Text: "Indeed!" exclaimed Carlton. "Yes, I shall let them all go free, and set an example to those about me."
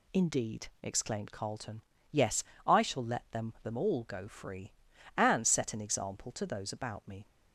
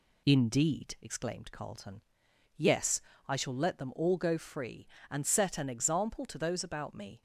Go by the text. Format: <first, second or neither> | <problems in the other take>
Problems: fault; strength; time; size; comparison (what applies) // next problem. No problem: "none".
second | says "them" twice; at 3.6 s